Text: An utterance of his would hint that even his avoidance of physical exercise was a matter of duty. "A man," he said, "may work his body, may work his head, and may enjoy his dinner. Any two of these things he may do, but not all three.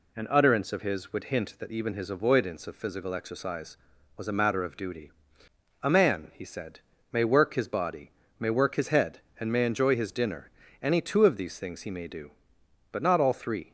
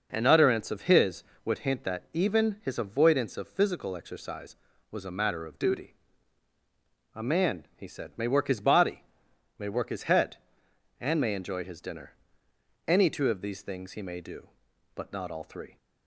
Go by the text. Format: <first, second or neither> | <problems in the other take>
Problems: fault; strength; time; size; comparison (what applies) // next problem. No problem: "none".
neither | none